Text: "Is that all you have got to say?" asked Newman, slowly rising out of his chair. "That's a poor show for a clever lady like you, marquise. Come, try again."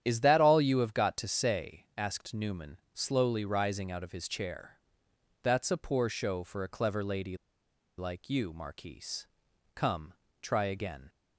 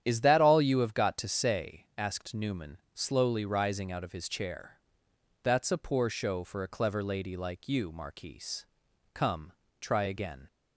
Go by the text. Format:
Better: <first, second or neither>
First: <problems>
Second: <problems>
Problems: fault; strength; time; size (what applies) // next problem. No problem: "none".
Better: second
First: starts louder than the rest; strong; until 1.0 s; 10 dB // pauses between "lady" and "like"; noticeable; at 7.3 s; 0.61 s long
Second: starts louder than the rest; strong; until 1.0 s; 10 dB